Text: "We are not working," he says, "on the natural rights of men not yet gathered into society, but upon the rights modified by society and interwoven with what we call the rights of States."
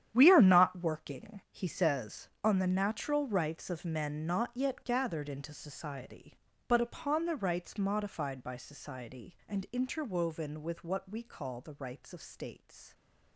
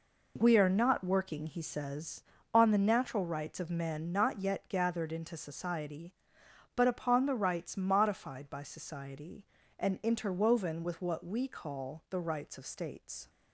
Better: second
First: gets quieter; strong; throughout; 13.5 dB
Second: none

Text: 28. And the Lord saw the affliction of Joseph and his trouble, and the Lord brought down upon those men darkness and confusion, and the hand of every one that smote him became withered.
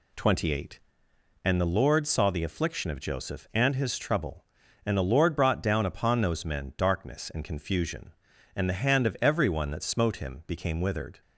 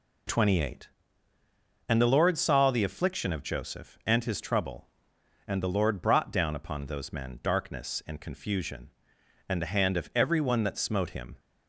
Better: first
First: none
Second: stops before "became withered"; at 11.3 s

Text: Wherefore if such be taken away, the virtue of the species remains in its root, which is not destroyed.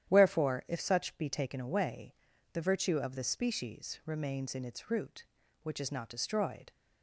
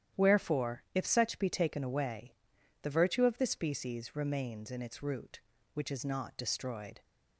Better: neither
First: starts louder than the rest; strong; until 1.1 s; 10.5 dB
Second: starts louder than the rest; strong; until 1.2 s; 10.5 dB

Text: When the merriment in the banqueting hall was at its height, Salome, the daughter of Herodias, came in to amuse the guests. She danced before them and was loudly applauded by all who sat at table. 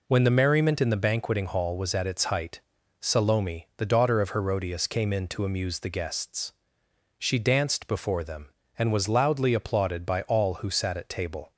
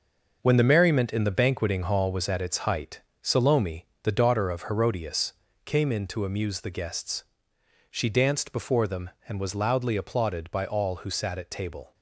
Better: first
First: none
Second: gets quieter; strong; throughout; 8.5 dB

